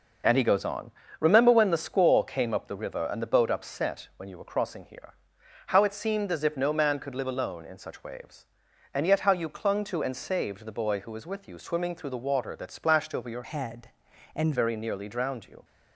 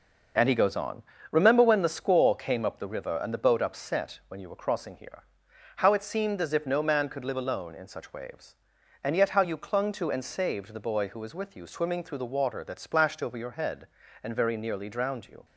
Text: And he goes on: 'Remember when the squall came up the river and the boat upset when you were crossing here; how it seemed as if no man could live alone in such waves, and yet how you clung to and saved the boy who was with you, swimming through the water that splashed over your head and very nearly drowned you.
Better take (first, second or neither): second